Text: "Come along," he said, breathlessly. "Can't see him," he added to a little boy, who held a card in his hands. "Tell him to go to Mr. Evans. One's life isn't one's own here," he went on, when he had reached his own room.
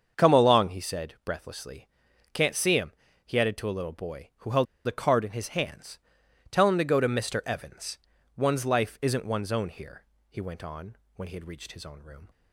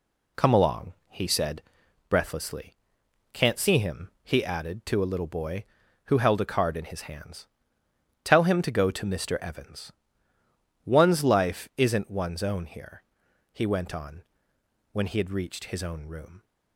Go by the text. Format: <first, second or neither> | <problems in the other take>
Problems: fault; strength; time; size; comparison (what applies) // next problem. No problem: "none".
second | starts louder than the rest; until 1.2 s; 6.5 dB // pauses between "held" and "a"; slight; at 4.6 s; 0.22 s long